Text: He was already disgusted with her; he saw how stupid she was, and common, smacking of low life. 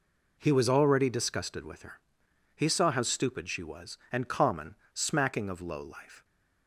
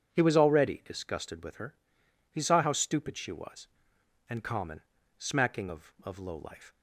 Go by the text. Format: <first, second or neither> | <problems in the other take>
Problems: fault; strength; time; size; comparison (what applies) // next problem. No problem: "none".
first | says "of" twice; at 6.0 s